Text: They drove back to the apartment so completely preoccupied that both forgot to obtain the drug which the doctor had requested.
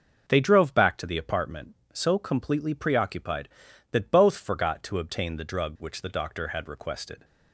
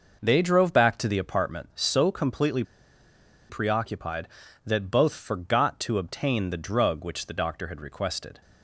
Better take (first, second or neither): first